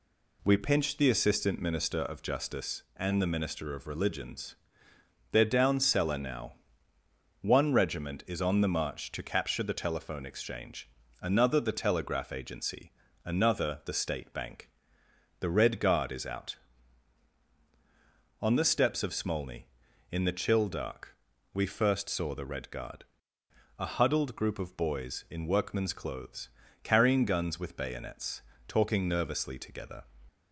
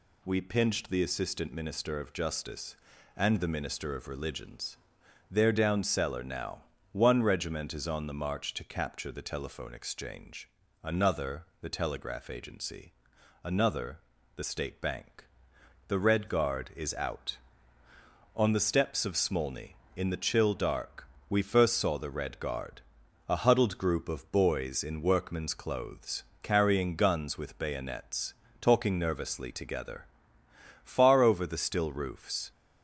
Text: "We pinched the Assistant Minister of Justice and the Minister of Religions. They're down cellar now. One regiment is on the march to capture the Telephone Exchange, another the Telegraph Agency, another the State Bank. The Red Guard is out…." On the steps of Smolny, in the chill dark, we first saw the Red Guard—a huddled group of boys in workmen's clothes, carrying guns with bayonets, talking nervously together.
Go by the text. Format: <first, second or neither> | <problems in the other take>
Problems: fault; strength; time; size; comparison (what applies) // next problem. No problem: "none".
first | pauses between "another" and "the"; at 13.9 s; 0.38 s long // goes on to say "Far over the still roofs"; strong; from 30.8 s on; 1.6 s long